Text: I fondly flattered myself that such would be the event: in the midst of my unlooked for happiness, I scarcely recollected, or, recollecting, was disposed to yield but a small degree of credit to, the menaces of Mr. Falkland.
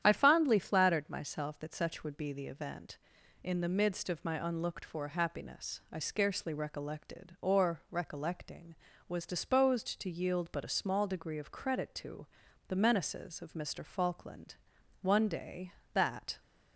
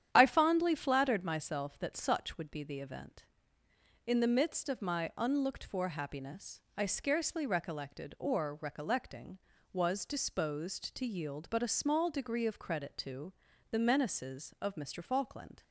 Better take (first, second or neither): second